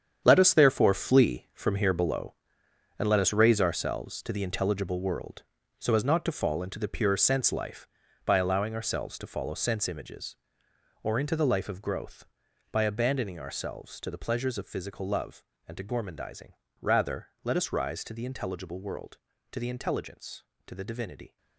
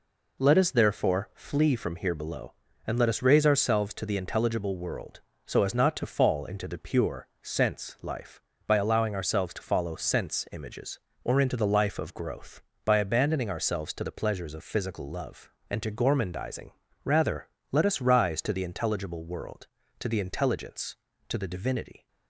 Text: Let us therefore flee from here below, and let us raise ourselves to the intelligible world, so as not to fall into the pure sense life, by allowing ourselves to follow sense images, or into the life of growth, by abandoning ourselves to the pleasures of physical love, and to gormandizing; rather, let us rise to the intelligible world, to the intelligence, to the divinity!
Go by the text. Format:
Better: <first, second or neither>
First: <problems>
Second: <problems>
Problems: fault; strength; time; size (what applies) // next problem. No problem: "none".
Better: second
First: gets quieter; strong; throughout; 11 dB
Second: none